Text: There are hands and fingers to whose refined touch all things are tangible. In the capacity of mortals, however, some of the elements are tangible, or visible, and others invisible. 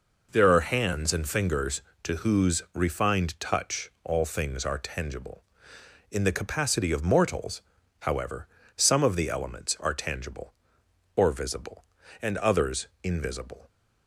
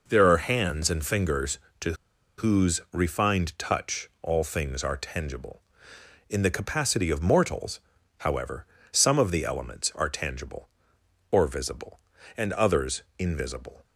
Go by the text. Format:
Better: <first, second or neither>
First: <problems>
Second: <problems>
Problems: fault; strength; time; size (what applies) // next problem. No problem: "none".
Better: first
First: pauses between "others" and "invisible"; slight; at 12.8 s; 0.16 s long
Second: pauses between "to" and "whose"; at 1.9 s; 0.44 s long // pauses between "others" and "invisible"; slight; at 13.0 s; 0.16 s long